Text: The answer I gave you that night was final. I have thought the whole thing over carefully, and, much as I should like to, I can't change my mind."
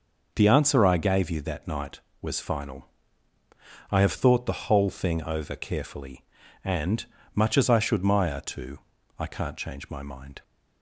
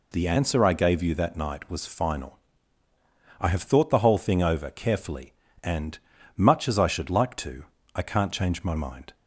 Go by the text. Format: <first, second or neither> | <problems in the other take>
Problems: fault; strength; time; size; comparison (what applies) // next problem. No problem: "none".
second | says "maya" for "like"; at 8.0 s